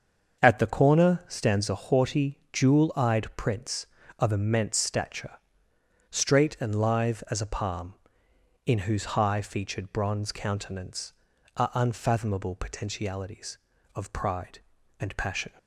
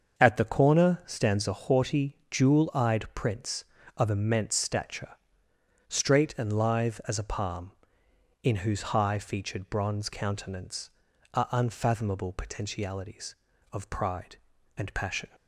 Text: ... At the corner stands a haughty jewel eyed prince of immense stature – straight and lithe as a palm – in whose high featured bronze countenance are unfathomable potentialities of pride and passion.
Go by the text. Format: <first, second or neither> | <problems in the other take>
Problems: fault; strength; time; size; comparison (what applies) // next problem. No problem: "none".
neither | starts louder than the rest; the same in both